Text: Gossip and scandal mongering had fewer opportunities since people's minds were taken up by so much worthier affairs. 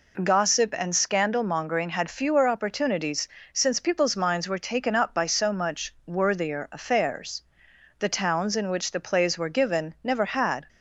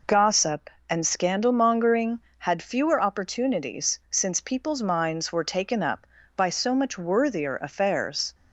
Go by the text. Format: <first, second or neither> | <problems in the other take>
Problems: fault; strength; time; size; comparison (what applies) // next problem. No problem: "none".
second | pauses between "opportunities" and "since"; slight; at 3.2 s; 0.24 s long // goes on to say "The towns in which the plays were given never had"; strong; from 7.9 s on; 2.7 s long